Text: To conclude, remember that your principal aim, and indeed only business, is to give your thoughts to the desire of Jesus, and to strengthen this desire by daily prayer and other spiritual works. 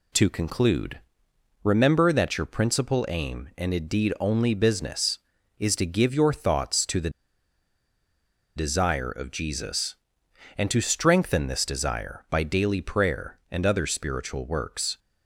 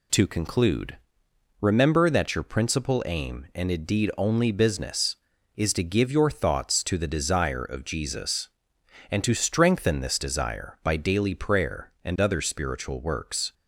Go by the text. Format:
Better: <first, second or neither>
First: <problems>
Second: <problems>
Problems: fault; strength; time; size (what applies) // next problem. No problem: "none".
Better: second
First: pauses between "the" and "desire"; strong; at 7.1 s; 1.4 s long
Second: none